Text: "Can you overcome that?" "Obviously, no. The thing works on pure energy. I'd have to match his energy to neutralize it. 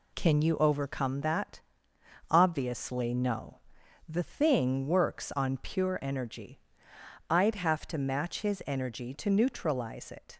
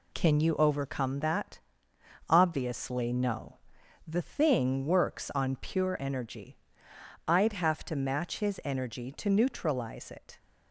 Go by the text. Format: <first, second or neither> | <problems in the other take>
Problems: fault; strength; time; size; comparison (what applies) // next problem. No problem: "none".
neither | none